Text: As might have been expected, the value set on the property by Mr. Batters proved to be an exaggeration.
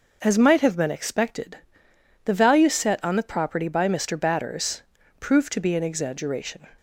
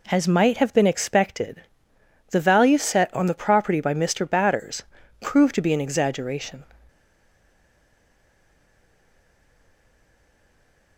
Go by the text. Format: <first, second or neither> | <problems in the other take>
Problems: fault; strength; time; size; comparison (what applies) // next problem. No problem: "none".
first | pauses between "Batters" and "proved"; slight; at 4.8 s; 0.36 s long; also in the first // stays silent after the last word; strong; from 6.8 s on; 4.1 s long